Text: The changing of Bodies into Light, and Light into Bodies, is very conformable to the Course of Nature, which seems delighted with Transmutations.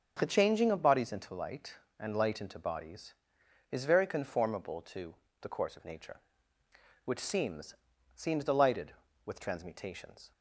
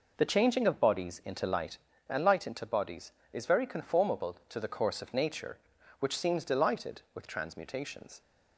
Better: second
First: starts louder than the rest; until 1.1 s; 6.5 dB // pauses between "to" and "the"; slight; at 5.1 s; 0.28 s long // says "seems" twice; at 8.1 s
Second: none

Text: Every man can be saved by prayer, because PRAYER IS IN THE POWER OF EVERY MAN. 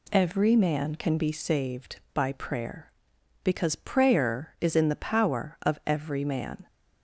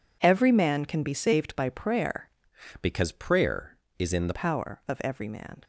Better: first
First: none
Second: changes voice from "because" to "THE"; from 2.8 to 4.3 s; 1.5 s long

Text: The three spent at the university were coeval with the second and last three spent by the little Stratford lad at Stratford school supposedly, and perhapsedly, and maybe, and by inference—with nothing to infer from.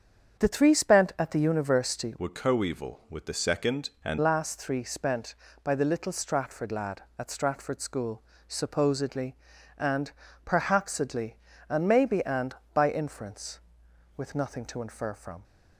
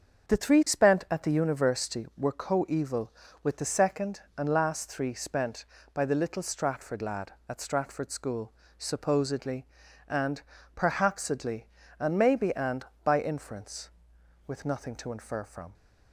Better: second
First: starts louder than the rest; strong; until 1.4 s; 7.5 dB // changes voice from "were" to "and"; from 2.1 to 4.1 s; 2.0 s long // pauses between "school" and "supposedly"; slight; at 8.2 s; 0.28 s long // pauses between "and" and "perhapsedly"; slight; at 10.1 s; 0.34 s long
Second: starts louder than the rest; until 1.3 s; 6.5 dB // pauses between "school" and "supposedly"; slight; at 8.5 s; 0.28 s long // pauses between "and" and "perhapsedly"; slight; at 10.4 s; 0.34 s long

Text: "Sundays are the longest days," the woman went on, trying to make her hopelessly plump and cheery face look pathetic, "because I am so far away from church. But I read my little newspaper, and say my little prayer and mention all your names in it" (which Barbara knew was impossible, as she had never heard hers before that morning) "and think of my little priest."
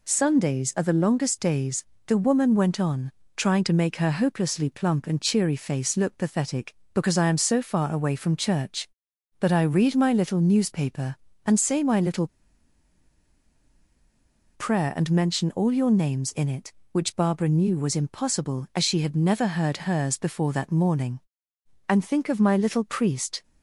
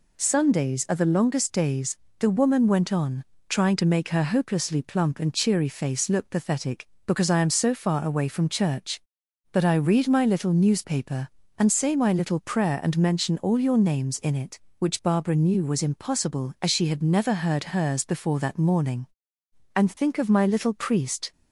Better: second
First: pauses between "little" and "prayer"; strong; at 12.2 s; 2.2 s long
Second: none

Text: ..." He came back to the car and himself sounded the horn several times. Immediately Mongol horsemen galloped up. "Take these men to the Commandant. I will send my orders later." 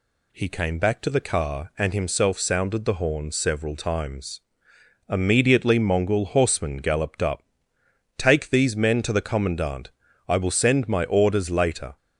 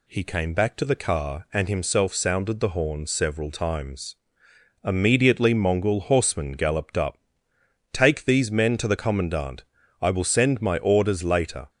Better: neither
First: none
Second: none

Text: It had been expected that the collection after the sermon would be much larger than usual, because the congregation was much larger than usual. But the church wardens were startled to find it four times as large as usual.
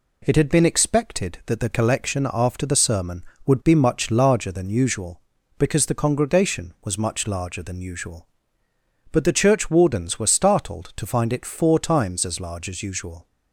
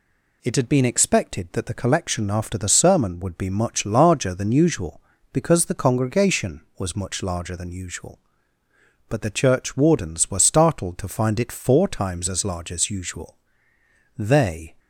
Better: first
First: none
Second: goes on to say "They"; from 14.1 s on; 0.58 s long

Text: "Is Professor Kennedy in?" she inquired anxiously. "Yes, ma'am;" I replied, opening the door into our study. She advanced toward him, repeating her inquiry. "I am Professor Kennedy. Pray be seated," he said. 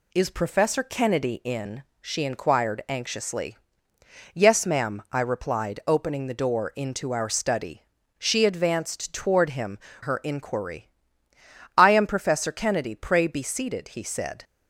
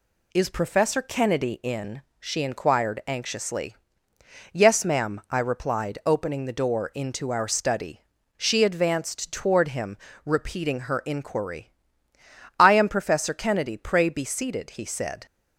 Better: second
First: skips "repeating"; at 9.9 s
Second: none

